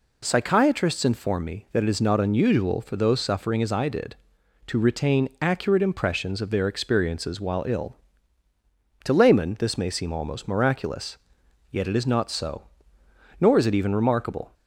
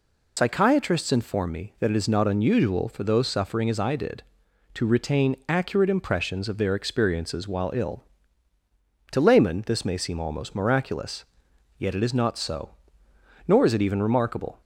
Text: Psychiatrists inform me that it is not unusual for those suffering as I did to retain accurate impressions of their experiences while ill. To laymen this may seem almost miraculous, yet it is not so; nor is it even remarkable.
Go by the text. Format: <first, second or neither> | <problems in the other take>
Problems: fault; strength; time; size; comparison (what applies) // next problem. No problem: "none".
first | loses the start of "Psychiatrists"; at 0.3 s; 70 ms